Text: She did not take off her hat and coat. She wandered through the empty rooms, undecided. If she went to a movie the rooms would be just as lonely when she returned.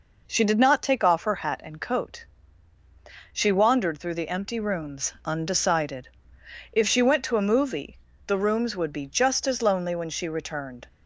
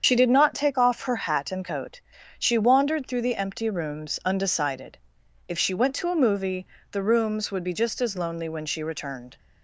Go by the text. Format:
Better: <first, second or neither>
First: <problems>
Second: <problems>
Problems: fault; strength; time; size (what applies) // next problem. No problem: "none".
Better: first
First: pauses between "movie" and "the"; slight; at 7.9 s; 0.26 s long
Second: loses the start of "She"; at 0.0 s; 60 ms // starts louder than the rest; strong; until 1.0 s; 7.5 dB // pauses between "movie" and "the"; slight; at 6.6 s; 0.24 s long